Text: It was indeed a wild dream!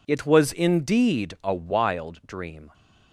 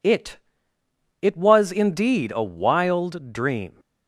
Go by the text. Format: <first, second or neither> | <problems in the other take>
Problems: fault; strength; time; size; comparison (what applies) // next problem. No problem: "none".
first | says "It" twice; at 1.2 s